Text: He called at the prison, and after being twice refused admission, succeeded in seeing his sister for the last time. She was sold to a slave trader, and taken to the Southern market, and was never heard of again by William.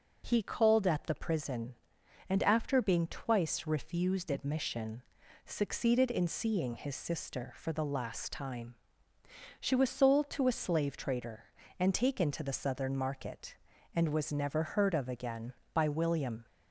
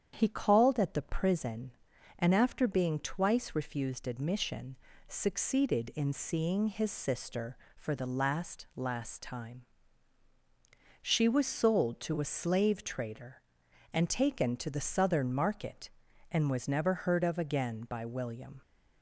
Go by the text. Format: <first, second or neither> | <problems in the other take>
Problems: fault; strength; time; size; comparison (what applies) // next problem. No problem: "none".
first | starts louder than the rest; strong; until 1.1 s; 8.5 dB // says "last" twice; at 8.7 s